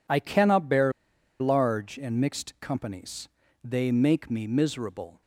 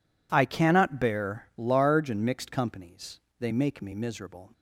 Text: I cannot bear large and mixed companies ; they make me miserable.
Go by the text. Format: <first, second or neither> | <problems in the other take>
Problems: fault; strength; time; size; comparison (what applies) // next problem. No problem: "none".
second | pauses between "bear" and "large"; noticeable; at 0.9 s; 0.48 s long